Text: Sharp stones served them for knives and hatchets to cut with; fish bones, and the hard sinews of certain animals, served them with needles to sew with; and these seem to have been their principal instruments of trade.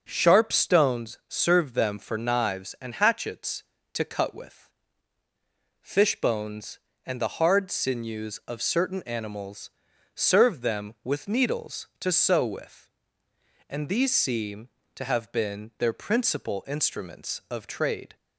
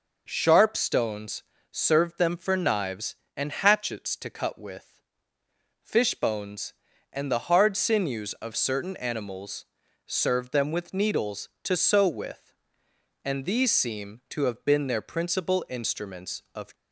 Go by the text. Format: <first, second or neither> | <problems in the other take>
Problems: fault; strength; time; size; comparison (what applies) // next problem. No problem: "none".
first | pauses between "stones" and "served"; slight; at 1.4 s; 0.30 s long // stops before "trade"; at 16.7 s